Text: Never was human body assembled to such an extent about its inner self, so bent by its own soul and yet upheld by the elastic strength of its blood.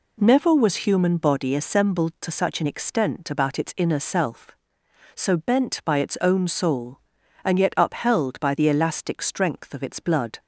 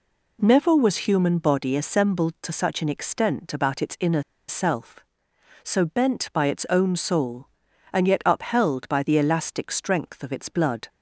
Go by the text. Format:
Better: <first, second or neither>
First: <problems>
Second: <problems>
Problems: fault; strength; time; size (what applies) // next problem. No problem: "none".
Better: first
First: none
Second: pauses between "inner" and "self"; slight; at 4.2 s; 0.26 s long